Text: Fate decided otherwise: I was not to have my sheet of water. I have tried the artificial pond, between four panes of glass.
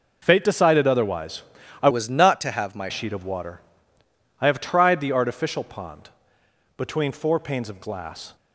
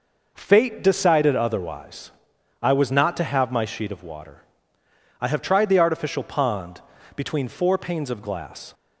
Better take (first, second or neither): second